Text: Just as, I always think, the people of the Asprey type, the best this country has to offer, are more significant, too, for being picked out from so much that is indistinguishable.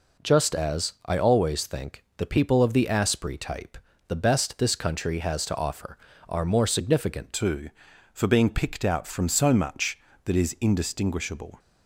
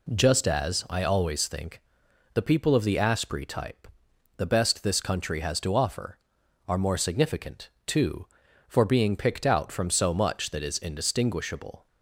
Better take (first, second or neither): second